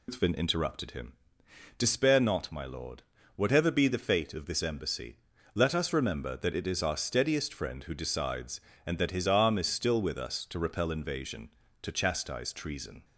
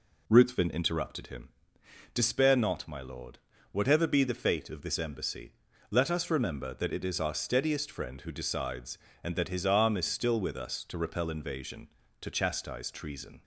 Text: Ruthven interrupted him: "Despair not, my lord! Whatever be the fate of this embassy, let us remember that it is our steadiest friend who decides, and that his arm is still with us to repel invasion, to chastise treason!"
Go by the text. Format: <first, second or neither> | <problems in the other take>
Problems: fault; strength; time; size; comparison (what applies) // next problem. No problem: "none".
second | loses the start of "Ruthven"; at 0.0 s; 170 ms